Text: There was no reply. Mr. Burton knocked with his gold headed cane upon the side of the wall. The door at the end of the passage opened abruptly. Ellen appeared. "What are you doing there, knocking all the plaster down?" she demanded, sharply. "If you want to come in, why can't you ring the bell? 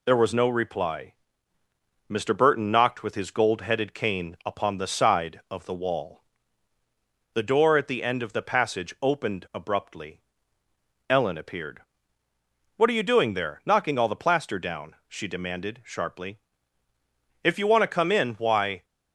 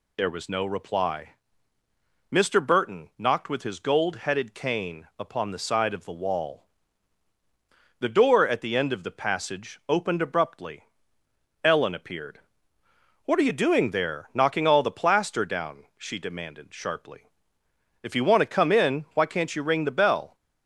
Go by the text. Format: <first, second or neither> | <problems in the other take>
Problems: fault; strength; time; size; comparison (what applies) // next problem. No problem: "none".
second | stops before "can't you ring the bell"; at 18.8 s